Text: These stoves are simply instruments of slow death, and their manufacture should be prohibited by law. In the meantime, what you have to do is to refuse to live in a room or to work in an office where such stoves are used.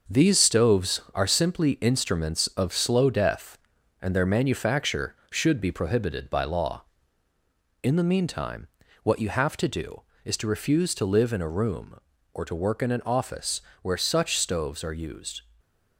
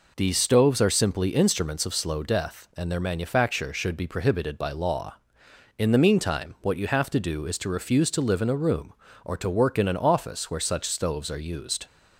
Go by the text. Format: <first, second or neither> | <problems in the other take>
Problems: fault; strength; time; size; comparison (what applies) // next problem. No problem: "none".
second | gets quieter; throughout; 6.5 dB // pauses between "office" and "where"; slight; at 13.6 s; 0.22 s long // stays silent after the last word; slight; from 15.4 s on; 0.5 s long